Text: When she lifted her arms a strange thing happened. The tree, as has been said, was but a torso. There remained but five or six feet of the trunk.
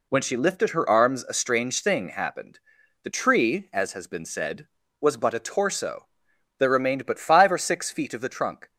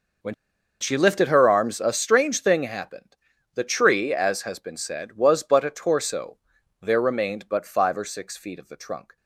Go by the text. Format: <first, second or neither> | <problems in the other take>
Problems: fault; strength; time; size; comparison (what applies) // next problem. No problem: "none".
first | pauses between "When" and "she"; noticeable; at 0.3 s; 0.46 s long